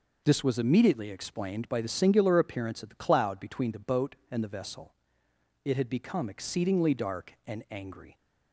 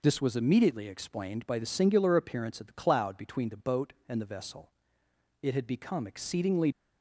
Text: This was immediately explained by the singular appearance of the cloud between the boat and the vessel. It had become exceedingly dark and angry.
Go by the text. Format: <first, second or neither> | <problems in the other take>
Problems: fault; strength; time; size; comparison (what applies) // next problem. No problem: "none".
first | stops before "dark and angry"; at 6.7 s